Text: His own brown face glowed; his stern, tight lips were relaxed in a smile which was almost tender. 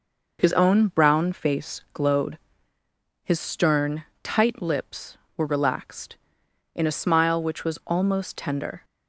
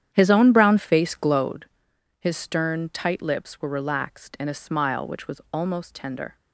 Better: first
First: none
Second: starts louder than the rest; strong; until 1.6 s; 9.5 dB

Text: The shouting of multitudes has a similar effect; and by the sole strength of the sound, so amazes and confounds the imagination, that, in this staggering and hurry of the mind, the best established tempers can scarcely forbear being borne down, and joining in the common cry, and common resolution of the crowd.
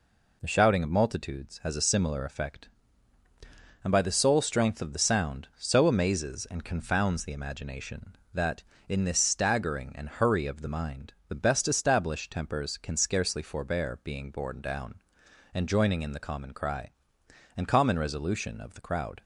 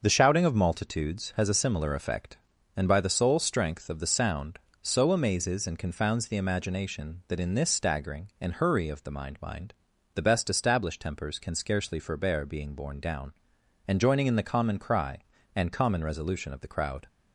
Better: first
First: none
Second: starts louder than the rest; noticeable; until 1.0 s; 6 dB // says "mind" twice; at 9.4 s

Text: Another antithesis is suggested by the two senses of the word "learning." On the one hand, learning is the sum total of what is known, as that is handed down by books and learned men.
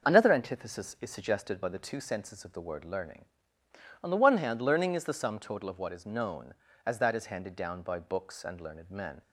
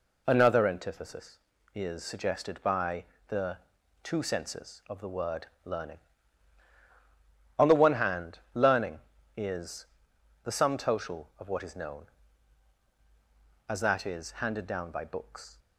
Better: first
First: none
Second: pauses between "by" and "the"; slight; at 3.0 s; 0.24 s long // pauses between "the" and "two"; noticeable; at 3.5 s; 0.46 s long // pauses between "word" and "learning"; slight; at 5.4 s; 0.18 s long // pauses between "is" and "the"; noticeable; at 9.8 s; 0.58 s long // stops before "and learned men"; at 15.5 s

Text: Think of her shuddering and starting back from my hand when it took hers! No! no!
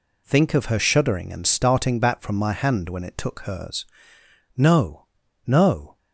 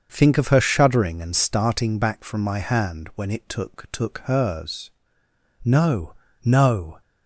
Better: first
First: none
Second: starts louder than the rest; until 1.1 s; 6.5 dB // says "took" twice; at 3.9 s

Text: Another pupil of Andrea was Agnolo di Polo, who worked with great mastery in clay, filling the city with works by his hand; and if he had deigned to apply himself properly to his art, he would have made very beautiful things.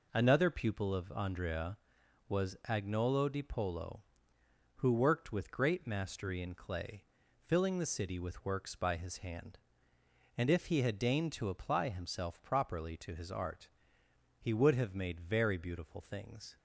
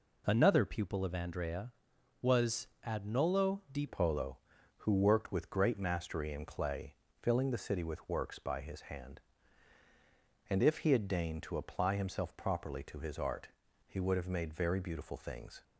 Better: first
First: none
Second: pauses between "was" and "Agnolo"; slight; at 2.6 s; 0.20 s long // changes voice at "Polo"; from 3.8 s on; 11.8 s long

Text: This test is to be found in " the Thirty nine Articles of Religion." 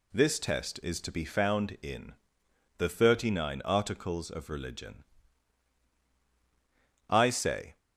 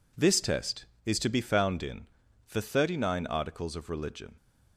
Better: second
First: goes on to say "I say"; noticeable; from 7.0 s on; 0.68 s long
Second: none

